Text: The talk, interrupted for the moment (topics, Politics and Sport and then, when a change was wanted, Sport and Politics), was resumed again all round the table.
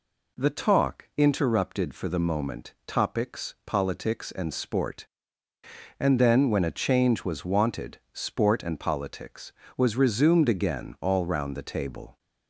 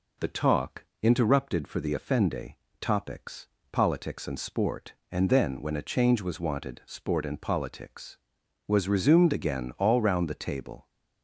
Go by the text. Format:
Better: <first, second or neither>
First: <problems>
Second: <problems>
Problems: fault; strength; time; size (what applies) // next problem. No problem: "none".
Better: first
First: none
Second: says "offende" for "moment"; at 1.9 s